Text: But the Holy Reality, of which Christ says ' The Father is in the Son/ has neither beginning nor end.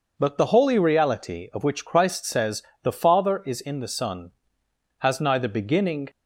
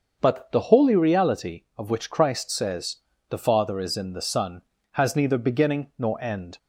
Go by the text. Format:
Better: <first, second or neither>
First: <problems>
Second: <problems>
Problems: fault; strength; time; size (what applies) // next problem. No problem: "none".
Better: second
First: starts louder than the rest; noticeable; until 1.1 s; 6 dB // stops before "nor end"; at 6.0 s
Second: none